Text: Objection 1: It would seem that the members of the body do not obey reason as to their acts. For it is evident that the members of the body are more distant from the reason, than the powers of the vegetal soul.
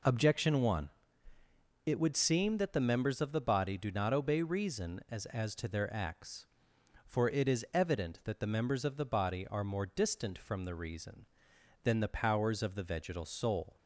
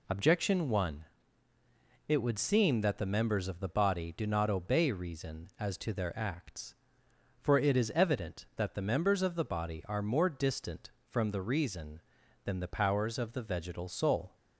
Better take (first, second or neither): second